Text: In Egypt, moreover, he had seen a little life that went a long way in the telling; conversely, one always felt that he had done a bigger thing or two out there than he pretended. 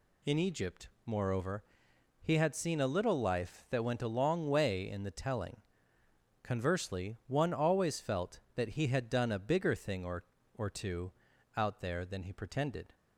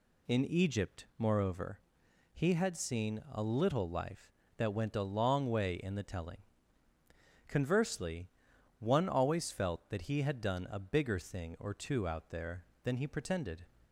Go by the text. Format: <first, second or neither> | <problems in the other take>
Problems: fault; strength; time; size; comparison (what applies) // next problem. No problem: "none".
second | says "or" twice; at 10.5 s // pauses between "two" and "out"; noticeable; at 11.1 s; 0.46 s long